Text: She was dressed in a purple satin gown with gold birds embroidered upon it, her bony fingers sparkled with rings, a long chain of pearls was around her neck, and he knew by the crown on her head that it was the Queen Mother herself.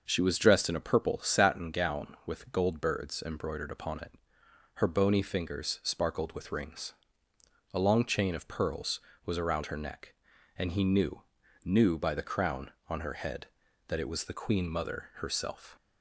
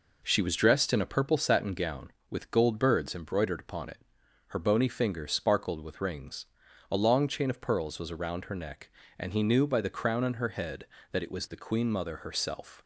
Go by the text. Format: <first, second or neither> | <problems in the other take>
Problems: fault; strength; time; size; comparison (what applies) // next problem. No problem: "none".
second | says "knew" twice; at 11.6 s